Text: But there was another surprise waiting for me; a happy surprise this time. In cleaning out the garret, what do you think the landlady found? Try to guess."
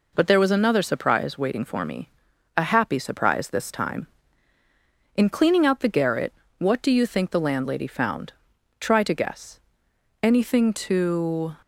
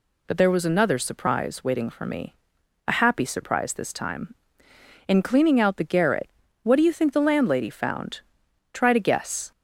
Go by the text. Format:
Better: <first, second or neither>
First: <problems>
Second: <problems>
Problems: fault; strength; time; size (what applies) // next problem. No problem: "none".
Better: second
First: goes on to say "Anything to"; from 10.2 s on; 1.3 s long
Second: none